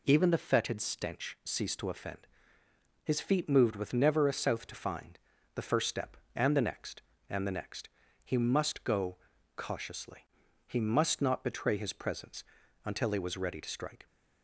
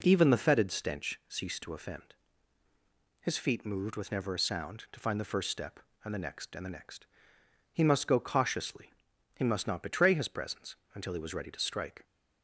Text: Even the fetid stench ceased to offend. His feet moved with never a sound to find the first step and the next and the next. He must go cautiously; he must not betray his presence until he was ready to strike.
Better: second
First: says "south" for "sound"; at 4.3 s // pauses between "find" and "the"; slight; at 5.1 s; 0.36 s long // pauses between "go" and "cautiously"; at 9.1 s; 0.40 s long // pauses between "presence" and "until"; at 12.4 s; 0.40 s long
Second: pauses between "presence" and "until"; slight; at 10.7 s; 0.20 s long

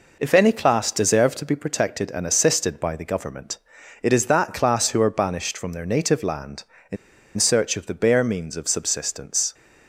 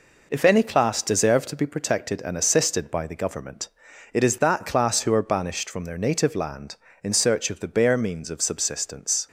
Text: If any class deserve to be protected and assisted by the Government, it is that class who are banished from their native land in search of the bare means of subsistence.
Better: second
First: pauses between "in" and "search"; at 6.9 s; 0.41 s long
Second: none

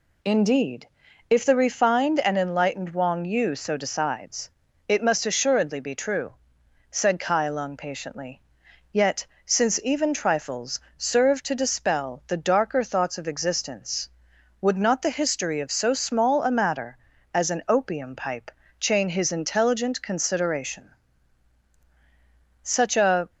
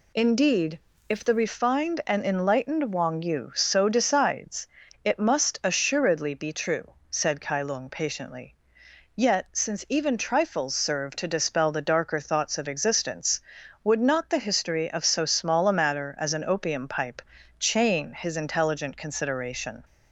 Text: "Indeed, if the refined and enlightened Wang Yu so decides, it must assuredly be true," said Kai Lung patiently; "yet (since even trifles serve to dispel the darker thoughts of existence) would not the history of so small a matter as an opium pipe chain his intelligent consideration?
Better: second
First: pauses between "trifles" and "serve"; slight; at 10.7 s; 0.16 s long // pauses between "pipe" and "chain"; slight; at 18.4 s; 0.30 s long // goes on to say "such a"; noticeable; from 22.6 s on; 0.66 s long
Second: pauses between "pipe" and "chain"; at 17.2 s; 0.38 s long

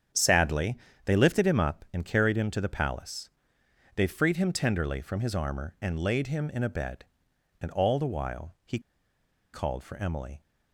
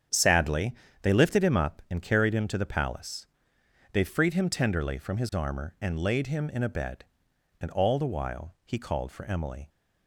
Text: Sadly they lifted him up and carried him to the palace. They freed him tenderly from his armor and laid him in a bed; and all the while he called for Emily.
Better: second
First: starts louder than the rest; strong; until 1.4 s; 8 dB // pauses between "Sadly" and "they"; slight; at 0.7 s; 0.30 s long // pauses between "he" and "called"; noticeable; at 8.7 s; 0.74 s long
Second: starts louder than the rest; strong; until 1.4 s; 8 dB // pauses between "Sadly" and "they"; slight; at 0.7 s; 0.30 s long

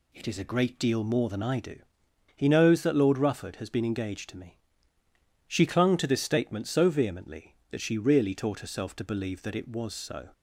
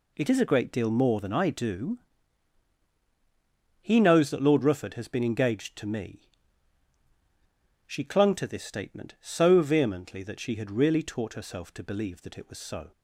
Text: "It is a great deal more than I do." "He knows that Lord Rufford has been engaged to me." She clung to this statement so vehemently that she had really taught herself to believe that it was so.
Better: second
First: skips "had"; at 7.9 s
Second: none

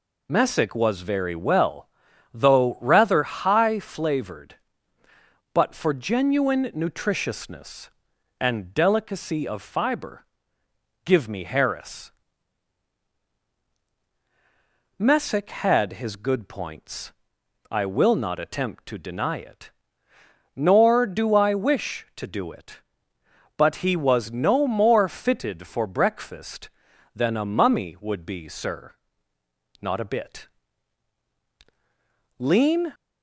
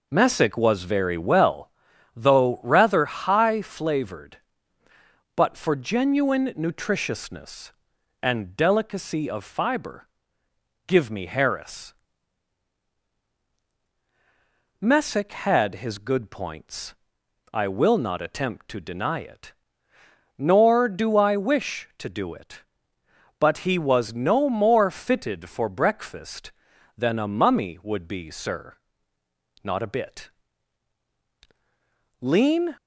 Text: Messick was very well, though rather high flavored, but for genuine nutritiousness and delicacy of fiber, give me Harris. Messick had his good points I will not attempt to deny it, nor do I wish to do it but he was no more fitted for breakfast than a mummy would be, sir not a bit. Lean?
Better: first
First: pauses between "points" and "I"; noticeable; at 17.1 s; 0.58 s long // pauses between "sir" and "not"; noticeable; at 28.9 s; 0.88 s long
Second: starts louder than the rest; noticeable; until 1.8 s; 4.5 dB // pauses between "points" and "I"; noticeable; at 16.9 s; 0.58 s long // pauses between "sir" and "not"; noticeable; at 28.7 s; 0.88 s long

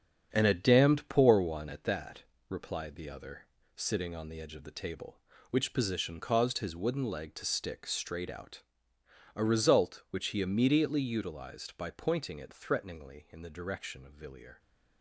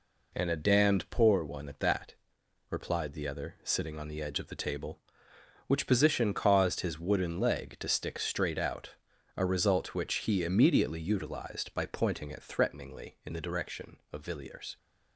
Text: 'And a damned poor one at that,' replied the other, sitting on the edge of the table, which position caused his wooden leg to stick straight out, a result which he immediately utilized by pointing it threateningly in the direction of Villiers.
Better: second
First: gets quieter; strong; throughout; 7 dB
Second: none

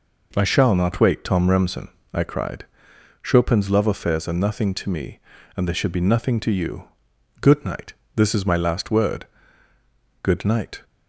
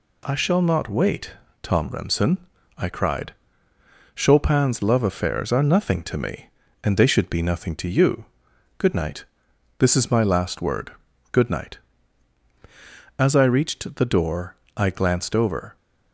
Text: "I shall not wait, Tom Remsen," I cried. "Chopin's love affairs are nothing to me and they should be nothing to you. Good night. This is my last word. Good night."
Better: first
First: none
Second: goes on to say "As I reached the door I glanced over"; strong; from 13.1 s on; 2.5 s long

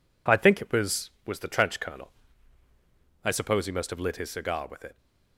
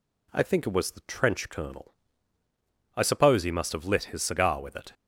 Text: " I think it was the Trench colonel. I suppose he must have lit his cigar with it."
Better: second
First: says "was" twice; at 1.2 s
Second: none

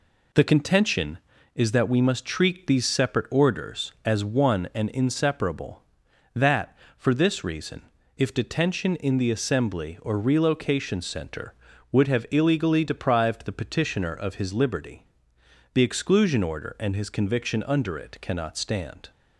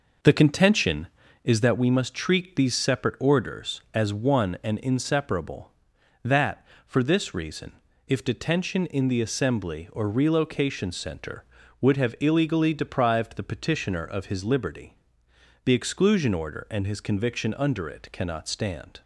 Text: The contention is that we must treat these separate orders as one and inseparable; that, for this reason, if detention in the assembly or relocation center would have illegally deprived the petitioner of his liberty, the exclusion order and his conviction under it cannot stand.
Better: first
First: none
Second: starts louder than the rest; noticeable; until 1.8 s; 5.5 dB

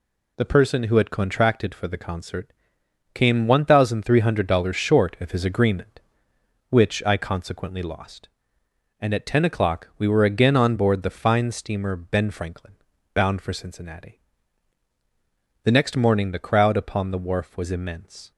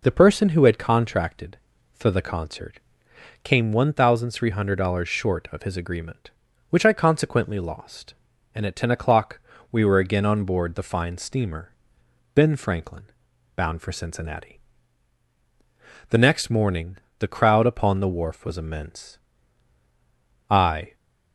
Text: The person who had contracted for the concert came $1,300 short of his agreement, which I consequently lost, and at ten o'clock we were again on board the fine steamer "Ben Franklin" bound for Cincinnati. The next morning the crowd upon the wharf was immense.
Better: first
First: pauses between "concert" and "came"; noticeable; at 2.5 s; 0.62 s long // pauses between "Franklin" and "bound"; at 12.7 s; 0.40 s long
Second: pauses between "concert" and "came"; noticeable; at 2.7 s; 0.62 s long // pauses between "o'clock" and "we"; slight; at 9.3 s; 0.32 s long // pauses between "steamer" and "Ben"; noticeable; at 11.7 s; 0.64 s long // pauses between "Franklin" and "bound"; noticeable; at 13.0 s; 0.50 s long // pauses between "morning" and "the"; slight; at 16.9 s; 0.22 s long // goes on to say "I"; slight; from 20.5 s on; 0.44 s long

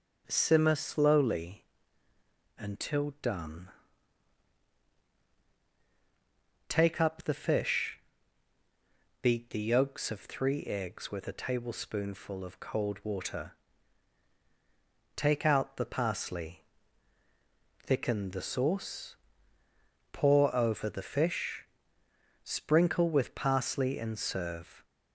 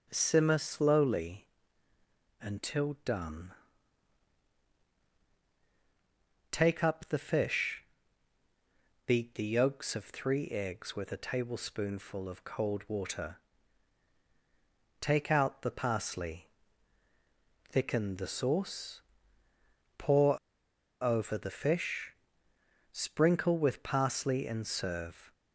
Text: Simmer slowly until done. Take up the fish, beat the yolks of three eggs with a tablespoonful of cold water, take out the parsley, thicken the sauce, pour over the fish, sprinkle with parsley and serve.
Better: first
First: starts louder than the rest; until 1.2 s; 6 dB // pauses between "slowly" and "until"; noticeable; at 1.6 s; 0.92 s long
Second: starts louder than the rest; until 1.1 s; 6 dB // pauses between "slowly" and "until"; noticeable; at 1.4 s; 0.92 s long // pauses between "pour" and "over"; noticeable; at 20.3 s; 0.64 s long

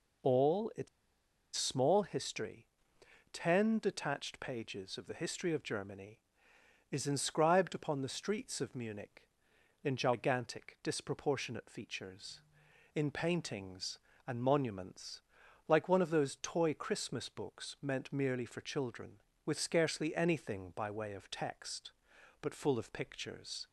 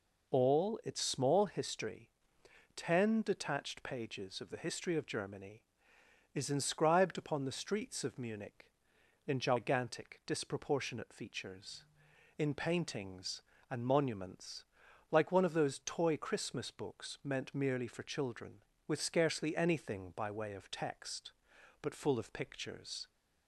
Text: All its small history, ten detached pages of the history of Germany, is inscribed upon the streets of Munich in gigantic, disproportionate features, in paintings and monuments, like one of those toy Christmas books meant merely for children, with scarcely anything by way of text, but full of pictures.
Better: second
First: pauses between "its" and "small"; noticeable; at 0.8 s; 0.67 s long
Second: none

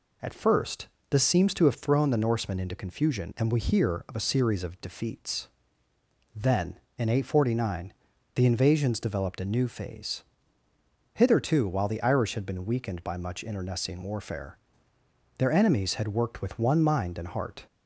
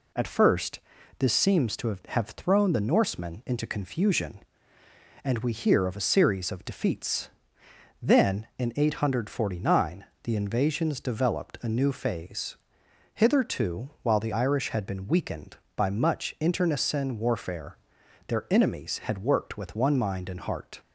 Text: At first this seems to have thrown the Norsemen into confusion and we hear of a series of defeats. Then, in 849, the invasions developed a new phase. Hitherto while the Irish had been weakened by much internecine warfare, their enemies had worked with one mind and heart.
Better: first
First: pauses between "first" and "this"; slight; at 0.8 s; 0.22 s long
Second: pauses between "first" and "this"; at 0.8 s; 0.38 s long // says "have" twice; at 2.0 s

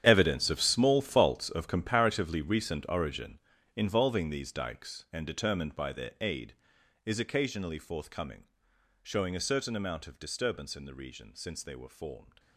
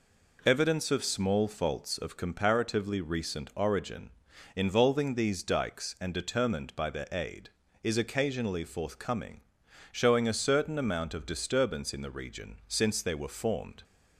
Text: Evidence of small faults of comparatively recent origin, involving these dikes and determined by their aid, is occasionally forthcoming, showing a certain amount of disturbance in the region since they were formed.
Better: second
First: gets quieter; strong; throughout; 15 dB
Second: none

